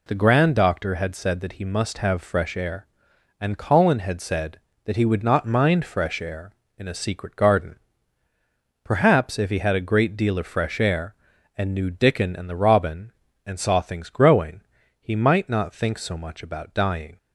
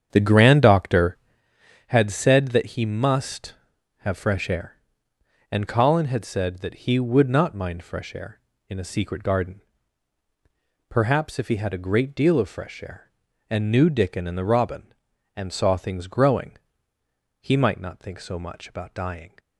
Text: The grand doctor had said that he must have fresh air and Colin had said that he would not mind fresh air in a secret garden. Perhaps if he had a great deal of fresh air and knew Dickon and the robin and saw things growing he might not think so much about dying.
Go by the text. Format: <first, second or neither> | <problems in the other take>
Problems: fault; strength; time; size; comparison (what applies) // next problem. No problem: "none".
first | starts louder than the rest; strong; until 1.5 s; 8 dB // pauses between "growing" and "he"; noticeable; at 16.5 s; 0.86 s long; also in the first